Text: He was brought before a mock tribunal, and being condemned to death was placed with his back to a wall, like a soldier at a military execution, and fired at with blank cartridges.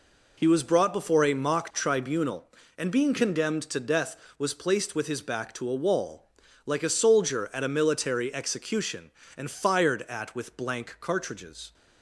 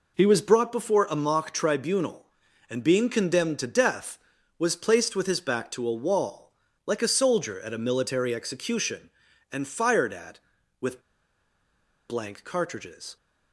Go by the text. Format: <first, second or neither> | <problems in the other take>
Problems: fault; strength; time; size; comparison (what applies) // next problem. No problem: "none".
first | pauses between "with" and "blank"; at 11.0 s; 1.0 s long